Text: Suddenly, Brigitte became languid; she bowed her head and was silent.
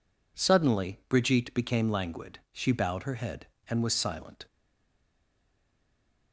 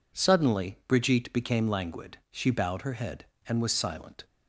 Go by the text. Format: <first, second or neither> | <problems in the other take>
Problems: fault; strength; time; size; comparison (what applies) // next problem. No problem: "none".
second | stays silent after the last word; noticeable; from 4.4 s on; 1.9 s long